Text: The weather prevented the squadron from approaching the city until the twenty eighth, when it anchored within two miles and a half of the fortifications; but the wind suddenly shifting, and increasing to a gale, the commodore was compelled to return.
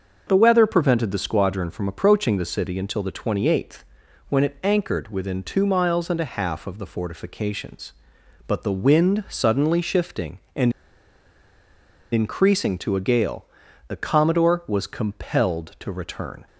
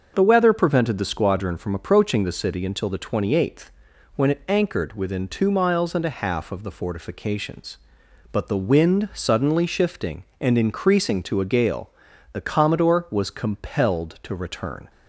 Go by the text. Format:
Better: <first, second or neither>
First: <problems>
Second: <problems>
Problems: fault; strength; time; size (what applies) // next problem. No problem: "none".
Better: second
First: starts louder than the rest; until 1.2 s; 6.5 dB // pauses between "and" and "increasing"; strong; at 10.7 s; 1.4 s long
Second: starts louder than the rest; until 1.1 s; 6.5 dB